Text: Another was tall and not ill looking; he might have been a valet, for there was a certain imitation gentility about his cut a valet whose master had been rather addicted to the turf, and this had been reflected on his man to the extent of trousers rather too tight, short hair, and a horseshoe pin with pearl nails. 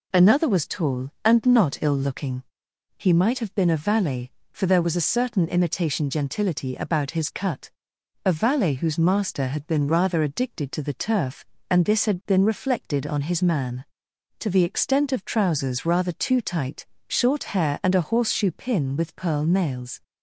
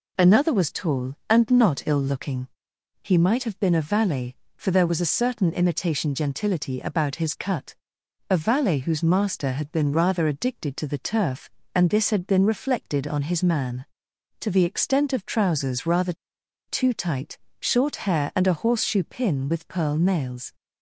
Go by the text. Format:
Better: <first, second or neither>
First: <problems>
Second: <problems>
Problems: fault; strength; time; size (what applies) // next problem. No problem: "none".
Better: first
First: pauses between "cut" and "a"; noticeable; at 7.6 s; 0.56 s long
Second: pauses between "cut" and "a"; noticeable; at 7.7 s; 0.56 s long // pauses between "rather" and "too"; noticeable; at 16.1 s; 0.54 s long